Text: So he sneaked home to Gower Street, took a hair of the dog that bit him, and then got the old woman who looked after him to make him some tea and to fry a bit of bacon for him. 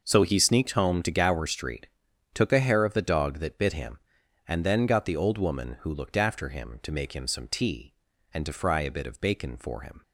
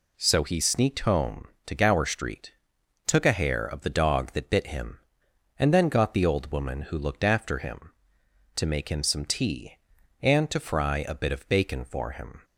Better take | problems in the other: neither | none

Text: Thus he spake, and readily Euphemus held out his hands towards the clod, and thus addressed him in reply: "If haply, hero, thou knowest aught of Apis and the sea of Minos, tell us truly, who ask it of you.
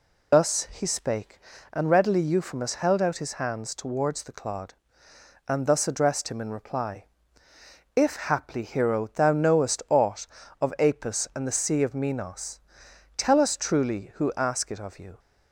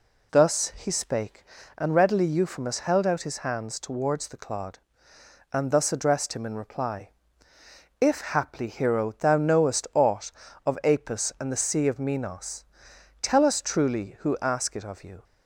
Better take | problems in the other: second | loses the start of "Thus"; at 0.3 s; 60 ms

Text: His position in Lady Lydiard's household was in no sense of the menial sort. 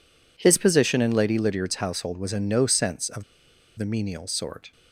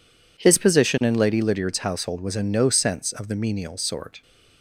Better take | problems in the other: second | pauses between "of" and "the"; noticeable; at 3.2 s; 0.53 s long

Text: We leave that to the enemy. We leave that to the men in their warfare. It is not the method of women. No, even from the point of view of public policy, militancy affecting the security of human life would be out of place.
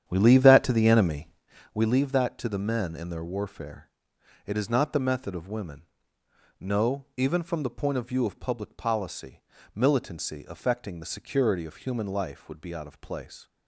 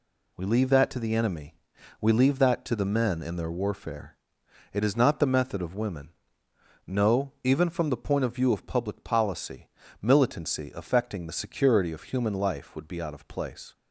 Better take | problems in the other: second | starts louder than the rest; strong; until 1.5 s; 9.5 dB

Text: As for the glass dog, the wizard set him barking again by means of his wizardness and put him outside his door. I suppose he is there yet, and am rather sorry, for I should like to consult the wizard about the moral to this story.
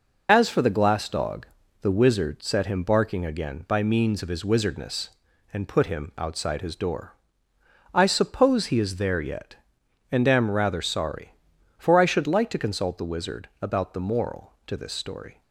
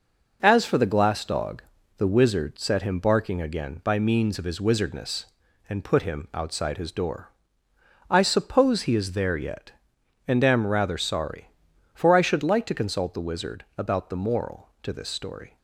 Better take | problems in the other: second | loses the start of "As"; at 0.2 s; 35 ms

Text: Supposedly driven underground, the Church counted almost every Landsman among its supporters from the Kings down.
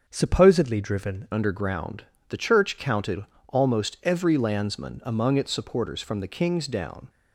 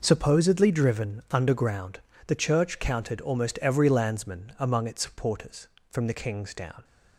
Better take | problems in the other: second | starts louder than the rest; until 1.0 s; 6.5 dB // changes voice at "underground"; from 1.3 s on; 5.7 s long // pauses between "counted" and "almost"; slight; at 3.2 s; 0.24 s long

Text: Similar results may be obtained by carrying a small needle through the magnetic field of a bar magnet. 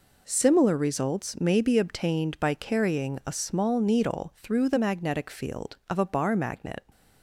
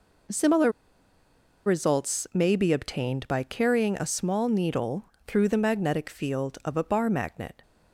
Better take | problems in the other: first | pauses between "Similar" and "results"; noticeable; at 0.7 s; 0.94 s long // pauses between "needle" and "through"; slight; at 5.0 s; 0.18 s long

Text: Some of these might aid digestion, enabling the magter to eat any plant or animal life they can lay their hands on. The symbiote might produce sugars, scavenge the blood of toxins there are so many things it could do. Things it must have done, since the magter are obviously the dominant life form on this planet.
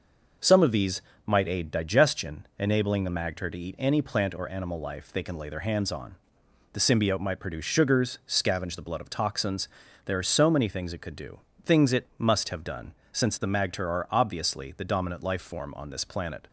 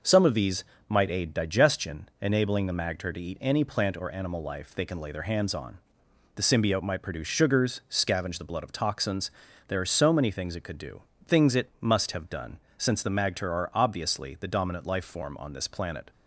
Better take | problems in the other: neither | pauses between "these" and "might"; slight; the same in both // pauses between "toxins" and "there"; slight; the same in both

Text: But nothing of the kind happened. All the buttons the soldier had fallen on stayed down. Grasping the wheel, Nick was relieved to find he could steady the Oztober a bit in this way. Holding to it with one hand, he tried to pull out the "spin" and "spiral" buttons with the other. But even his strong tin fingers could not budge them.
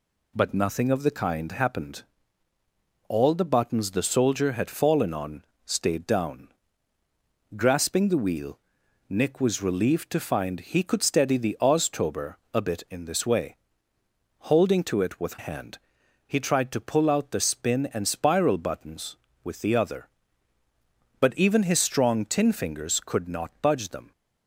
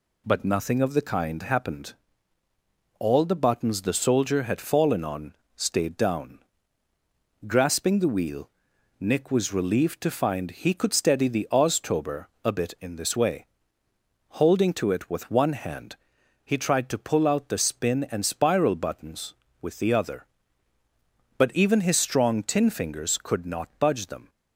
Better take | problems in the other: second | pauses between "on" and "stayed"; slight; at 5.4 s; 0.22 s long; slight in the second // pauses between "Oztober" and "a"; slight; at 12.3 s; 0.18 s long; slight in the second // skips "one"; at 15.3 s

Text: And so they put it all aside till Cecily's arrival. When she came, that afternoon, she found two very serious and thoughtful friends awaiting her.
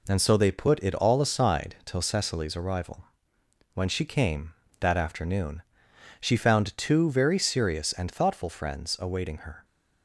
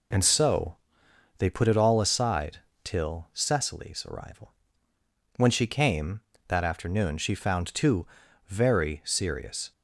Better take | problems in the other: first | pauses between "so" and "they"; noticeable; at 0.7 s; 0.62 s long // pauses between "aside" and "till"; slight; at 2.5 s; 0.26 s long // pauses between "two" and "very"; at 8.0 s; 0.42 s long // stops before "and thoughtful friends awaiting her"; at 9.7 s

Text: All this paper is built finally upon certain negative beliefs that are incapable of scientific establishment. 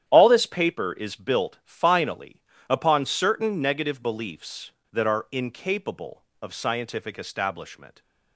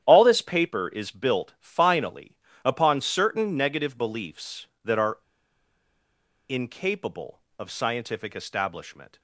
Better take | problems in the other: first | starts louder than the rest; strong; until 1.0 s; 10 dB; strong in the first // pauses between "finally" and "upon"; slight; at 2.3 s; 0.28 s long; slight in the first // pauses between "are" and "incapable"; strong; at 5.1 s; 1.3 s long

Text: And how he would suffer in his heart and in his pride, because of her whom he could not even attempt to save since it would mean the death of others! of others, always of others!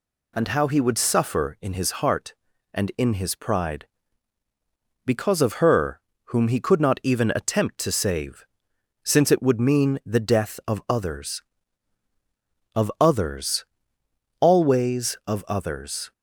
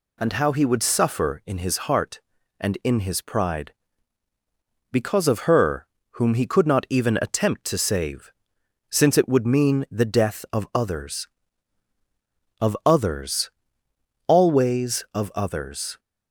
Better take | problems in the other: neither | pauses between "her" and "whom"; slight; the same in both // pauses between "save" and "since"; noticeable; the same in both

